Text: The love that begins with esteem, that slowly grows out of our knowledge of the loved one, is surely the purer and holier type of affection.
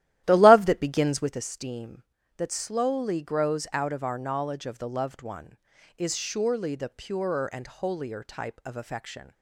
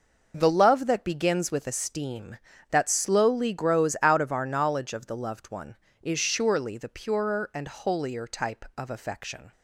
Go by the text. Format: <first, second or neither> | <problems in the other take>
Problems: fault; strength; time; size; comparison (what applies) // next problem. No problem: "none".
second | starts louder than the rest; strong; until 1.5 s; 13.5 dB